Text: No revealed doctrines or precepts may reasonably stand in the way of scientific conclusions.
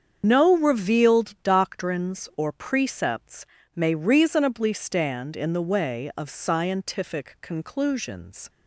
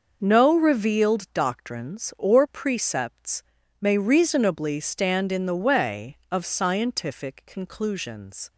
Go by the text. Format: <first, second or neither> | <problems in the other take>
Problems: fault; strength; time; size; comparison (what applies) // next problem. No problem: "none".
second | loses the start of "No"; at 0.2 s; 90 ms // starts louder than the rest; strong; until 1.2 s; 7.5 dB // pauses between "precepts" and "may"; slight; at 3.4 s; 0.32 s long; also in the second